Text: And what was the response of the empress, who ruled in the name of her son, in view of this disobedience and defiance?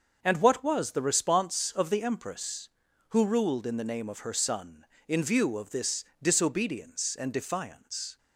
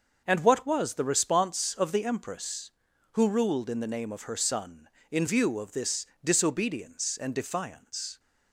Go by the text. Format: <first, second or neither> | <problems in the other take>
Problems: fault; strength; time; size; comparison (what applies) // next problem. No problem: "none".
neither | starts louder than the rest; the same in both // pauses between "this" and "disobedience"; slight; the same in both